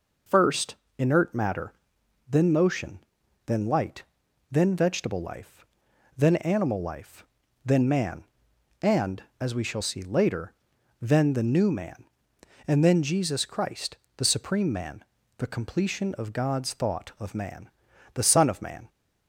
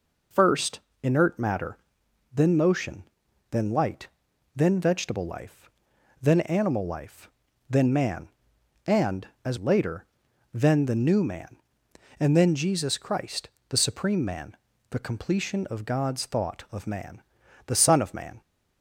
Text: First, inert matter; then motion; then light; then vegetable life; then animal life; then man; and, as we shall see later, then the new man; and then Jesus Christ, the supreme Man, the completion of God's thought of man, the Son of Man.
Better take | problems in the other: first | skips "we shall see"; at 9.5 s

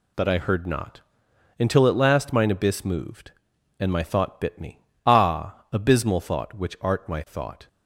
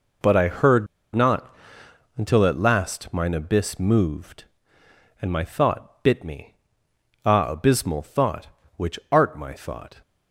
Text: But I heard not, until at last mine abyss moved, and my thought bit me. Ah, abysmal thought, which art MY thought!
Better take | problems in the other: first | pauses between "heard" and "not"; slight; at 0.8 s; 0.27 s long

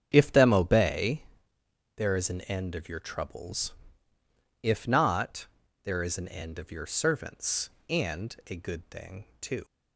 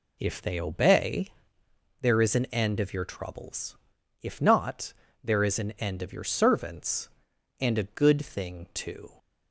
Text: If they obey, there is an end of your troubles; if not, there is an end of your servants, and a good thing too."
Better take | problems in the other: second | starts louder than the rest; strong; until 1.1 s; 8.5 dB // says "them" for "they"; at 0.3 s // pauses between "thing" and "too"; slight; at 9.2 s; 0.16 s long

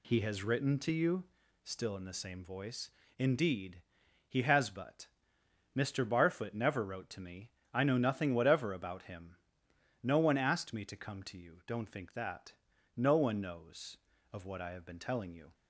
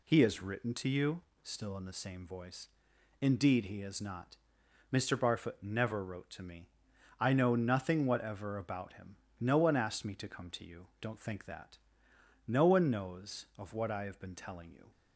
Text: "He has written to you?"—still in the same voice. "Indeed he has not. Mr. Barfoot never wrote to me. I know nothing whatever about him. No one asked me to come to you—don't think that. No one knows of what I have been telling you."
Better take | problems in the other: second | pauses between "Indeed" and "he"; noticeable; at 3.8 s; 0.46 s long // says "but" for "not"; at 4.6 s

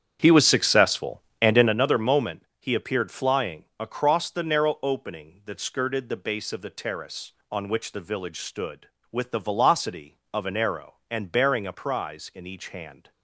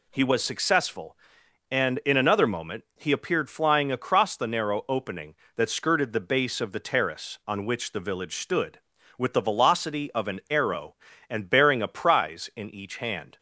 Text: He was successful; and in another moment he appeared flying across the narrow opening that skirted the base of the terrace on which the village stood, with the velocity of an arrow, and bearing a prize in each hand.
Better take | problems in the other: second | starts louder than the rest; strong; until 1.8 s; 8.5 dB // pauses between "moment" and "he"; slight; at 2.4 s; 0.16 s long

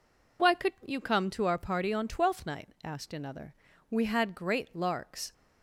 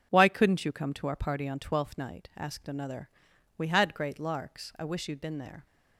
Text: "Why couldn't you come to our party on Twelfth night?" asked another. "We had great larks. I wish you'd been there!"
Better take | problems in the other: second | stops before "I wish you'd been there"; at 5.3 s

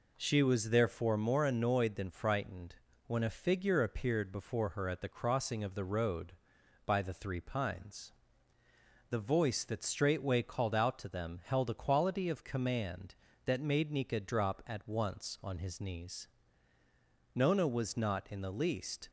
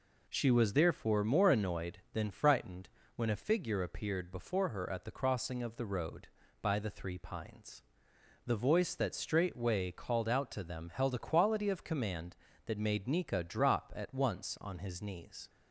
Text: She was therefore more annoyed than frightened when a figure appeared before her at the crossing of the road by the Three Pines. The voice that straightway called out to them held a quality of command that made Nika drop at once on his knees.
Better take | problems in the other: second | pauses between "frightened" and "when"; slight; at 2.7 s; 0.30 s long; slight in the second // goes on to say "Nona was not in the least"; strong; from 17.3 s on; 1.7 s long

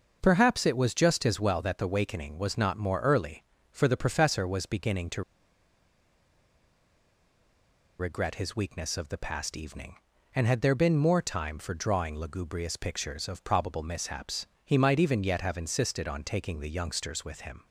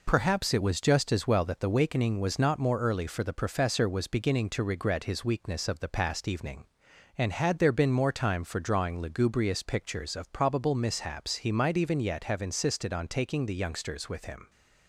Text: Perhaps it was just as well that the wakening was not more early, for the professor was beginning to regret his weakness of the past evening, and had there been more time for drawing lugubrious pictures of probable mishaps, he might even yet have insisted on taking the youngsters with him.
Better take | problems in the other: second | starts louder than the rest; noticeable; until 1.2 s; 6 dB // pauses between "to" and "regret"; strong; at 5.2 s; 2.7 s long

